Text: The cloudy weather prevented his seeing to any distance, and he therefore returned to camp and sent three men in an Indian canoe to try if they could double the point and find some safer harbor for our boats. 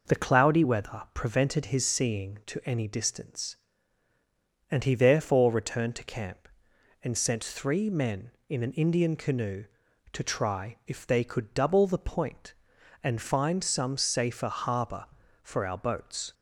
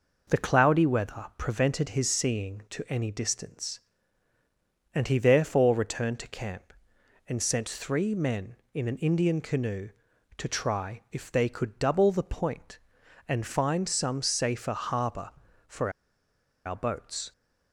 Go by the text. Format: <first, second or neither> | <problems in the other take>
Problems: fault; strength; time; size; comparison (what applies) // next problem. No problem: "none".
first | pauses between "for" and "our"; noticeable; at 15.9 s; 0.75 s long